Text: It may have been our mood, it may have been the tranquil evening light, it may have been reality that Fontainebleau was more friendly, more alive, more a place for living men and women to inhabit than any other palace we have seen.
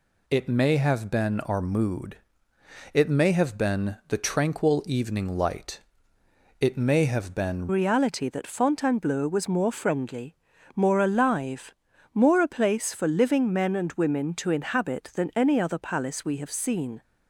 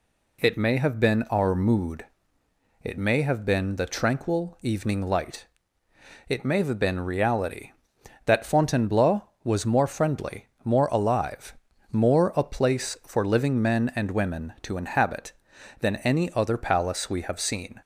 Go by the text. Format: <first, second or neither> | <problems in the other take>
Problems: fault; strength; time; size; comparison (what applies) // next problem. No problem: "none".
second | changes voice at "reality"; from 7.6 s on; 9.4 s long